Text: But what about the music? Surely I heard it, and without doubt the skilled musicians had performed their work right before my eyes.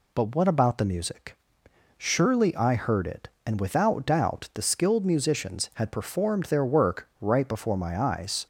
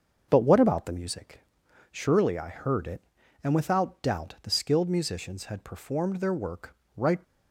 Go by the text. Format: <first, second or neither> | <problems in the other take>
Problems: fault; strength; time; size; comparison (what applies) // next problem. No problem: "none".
first | starts louder than the rest; until 1.3 s; 6.5 dB // pauses between "work" and "right"; slight; at 6.7 s; 0.20 s long // stops before "before my eyes"; at 7.2 s